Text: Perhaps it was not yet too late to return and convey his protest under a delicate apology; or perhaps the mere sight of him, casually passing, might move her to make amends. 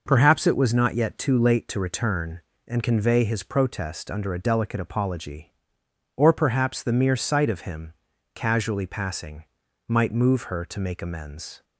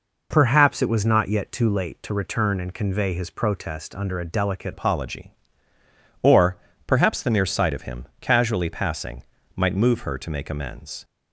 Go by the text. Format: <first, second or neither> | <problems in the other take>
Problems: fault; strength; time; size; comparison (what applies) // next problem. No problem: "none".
first | changes voice at "apology"; from 4.7 s on; 6.3 s long // pauses between "or" and "perhaps"; slight; at 6.5 s; 0.30 s long